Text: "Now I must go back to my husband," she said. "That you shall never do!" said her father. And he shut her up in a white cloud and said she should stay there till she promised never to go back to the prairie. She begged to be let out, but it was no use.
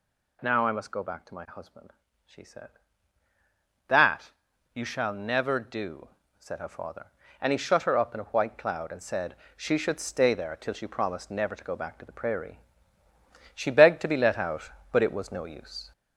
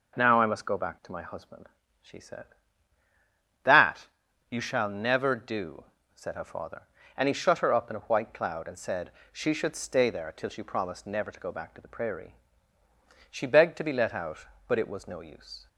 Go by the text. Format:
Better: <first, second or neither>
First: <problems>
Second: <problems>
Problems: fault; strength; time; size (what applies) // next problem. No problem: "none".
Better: second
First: gets louder; noticeable; throughout; 4.5 dB // pauses between "That" and "you"; at 4.3 s; 0.42 s long // pauses between "said" and "she"; slight; at 9.3 s; 0.20 s long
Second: pauses between "That" and "you"; at 4.0 s; 0.42 s long // pauses between "said" and "she"; slight; at 9.1 s; 0.20 s long